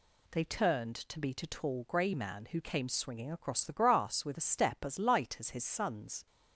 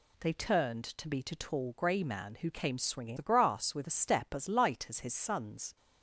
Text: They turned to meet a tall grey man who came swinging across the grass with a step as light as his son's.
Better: first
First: none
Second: skips "across"; at 3.1 s

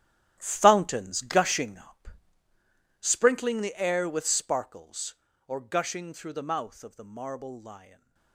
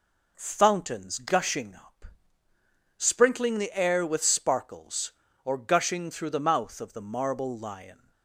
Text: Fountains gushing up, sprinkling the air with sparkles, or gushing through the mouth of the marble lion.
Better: second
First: gets quieter; strong; throughout; 15 dB // stays silent after the last word; slight; from 7.7 s on; 0.6 s long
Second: none

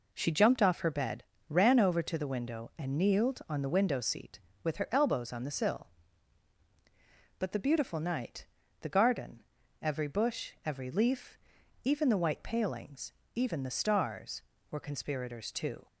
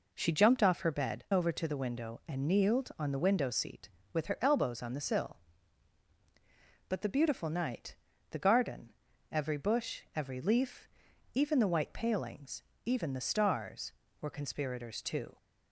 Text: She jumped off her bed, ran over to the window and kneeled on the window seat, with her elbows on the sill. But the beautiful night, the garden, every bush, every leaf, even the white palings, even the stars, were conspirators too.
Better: first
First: none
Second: skips "ran"; at 1.2 s

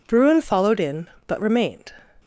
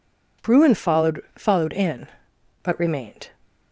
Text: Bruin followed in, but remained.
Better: first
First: none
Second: says "followed" twice; at 1.3 s

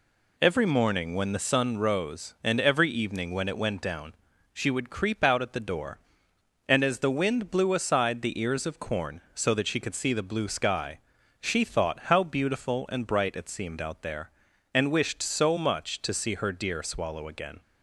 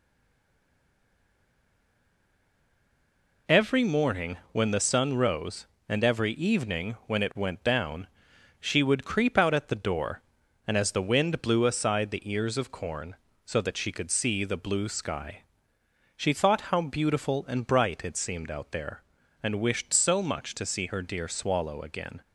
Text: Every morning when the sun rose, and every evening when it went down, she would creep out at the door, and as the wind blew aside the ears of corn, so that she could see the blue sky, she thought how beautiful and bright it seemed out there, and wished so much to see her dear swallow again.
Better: first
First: none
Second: stays silent before the first word; strong; until 3.4 s; 3.4 s long

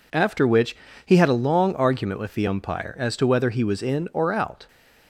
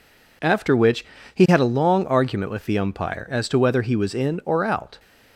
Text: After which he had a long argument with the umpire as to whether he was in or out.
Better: neither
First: pauses between "which" and "he"; slight; at 0.7 s; 0.28 s long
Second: pauses between "which" and "he"; slight; at 1.0 s; 0.28 s long

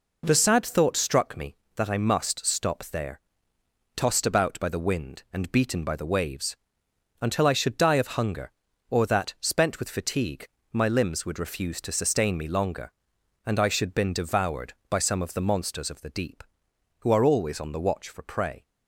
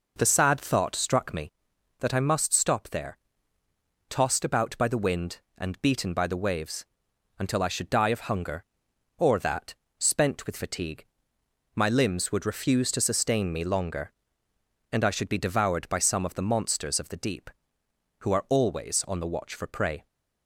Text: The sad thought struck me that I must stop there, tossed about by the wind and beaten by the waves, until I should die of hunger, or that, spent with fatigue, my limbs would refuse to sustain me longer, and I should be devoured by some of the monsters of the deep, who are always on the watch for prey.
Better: second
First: says "been" for "be"; at 13.9 s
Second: none

